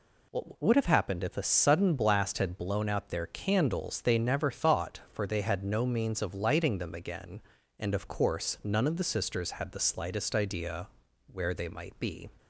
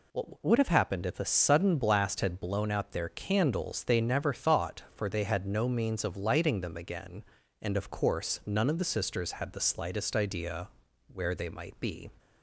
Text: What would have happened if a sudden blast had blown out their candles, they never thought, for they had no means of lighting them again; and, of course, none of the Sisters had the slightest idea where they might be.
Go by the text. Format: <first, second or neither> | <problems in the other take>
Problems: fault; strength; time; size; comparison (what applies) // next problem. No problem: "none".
neither | pauses between "idea" and "where"; the same in both